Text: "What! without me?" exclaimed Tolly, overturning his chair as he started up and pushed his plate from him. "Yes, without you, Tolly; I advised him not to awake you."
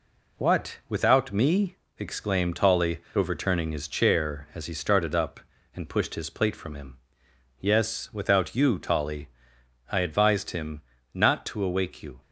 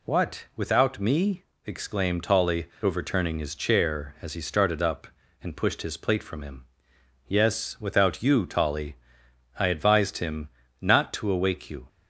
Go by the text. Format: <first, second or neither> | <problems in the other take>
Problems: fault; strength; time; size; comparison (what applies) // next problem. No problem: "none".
second | gets quieter; throughout; 3.5 dB // pauses between "him" and "not"; slight; at 10.8 s; 0.32 s long; slight in the second